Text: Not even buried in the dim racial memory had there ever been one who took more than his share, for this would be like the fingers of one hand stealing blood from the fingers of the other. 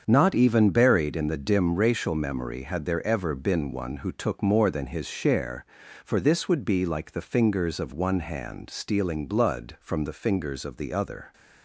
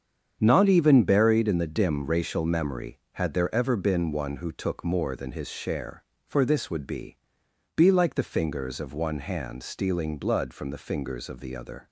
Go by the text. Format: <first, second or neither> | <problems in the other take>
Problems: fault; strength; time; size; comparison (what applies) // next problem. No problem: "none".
first | starts louder than the rest; strong; until 1.4 s; 7.5 dB; also in the first // says "be" twice; at 7.7 s